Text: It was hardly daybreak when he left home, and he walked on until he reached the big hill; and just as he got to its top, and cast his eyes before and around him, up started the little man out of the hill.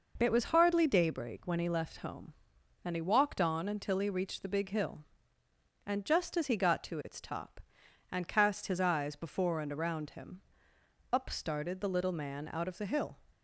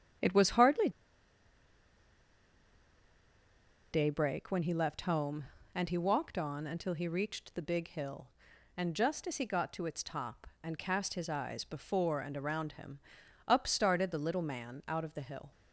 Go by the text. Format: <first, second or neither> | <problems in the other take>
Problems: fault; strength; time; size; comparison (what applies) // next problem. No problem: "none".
first | starts louder than the rest; strong; until 4.2 s; 9 dB // pauses between "hardly" and "daybreak"; strong; at 0.9 s; 3.0 s long